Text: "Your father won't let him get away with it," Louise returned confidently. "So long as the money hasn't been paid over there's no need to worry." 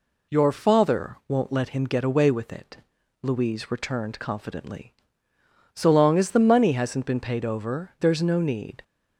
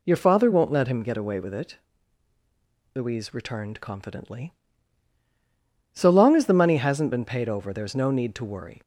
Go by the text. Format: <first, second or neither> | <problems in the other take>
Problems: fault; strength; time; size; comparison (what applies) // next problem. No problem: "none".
second | stops before "to worry"; at 8.8 s